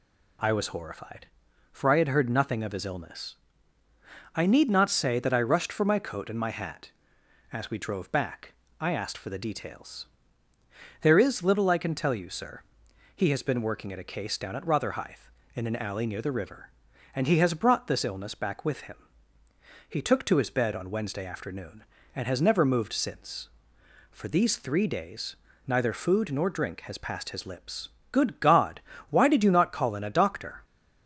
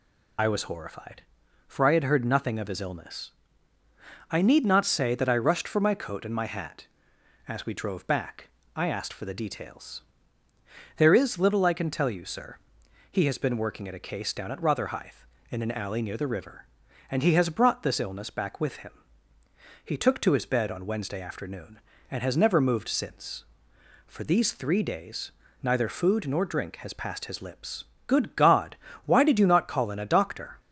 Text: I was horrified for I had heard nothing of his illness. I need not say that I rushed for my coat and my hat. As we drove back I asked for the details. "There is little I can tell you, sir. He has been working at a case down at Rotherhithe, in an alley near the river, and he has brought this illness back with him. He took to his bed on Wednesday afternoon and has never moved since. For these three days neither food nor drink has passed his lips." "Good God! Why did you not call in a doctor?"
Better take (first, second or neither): first